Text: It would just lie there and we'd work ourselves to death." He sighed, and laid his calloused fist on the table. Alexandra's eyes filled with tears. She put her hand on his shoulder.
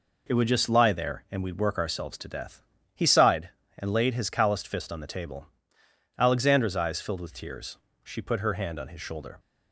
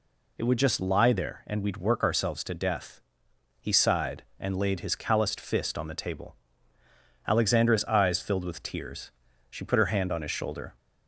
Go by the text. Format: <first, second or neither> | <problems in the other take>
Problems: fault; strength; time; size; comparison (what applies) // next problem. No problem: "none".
neither | none